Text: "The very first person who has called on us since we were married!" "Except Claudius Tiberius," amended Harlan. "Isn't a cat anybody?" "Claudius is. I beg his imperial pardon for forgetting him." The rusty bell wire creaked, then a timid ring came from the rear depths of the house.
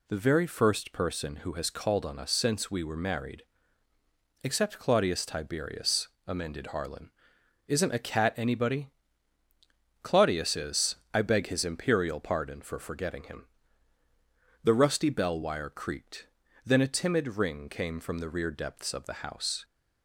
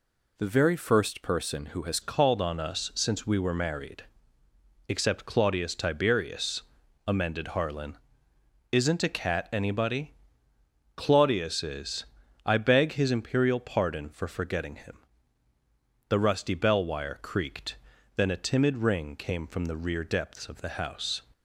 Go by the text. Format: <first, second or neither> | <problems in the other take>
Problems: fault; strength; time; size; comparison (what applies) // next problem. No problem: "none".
first | changes voice at "called"; from 2.0 s on; 19.2 s long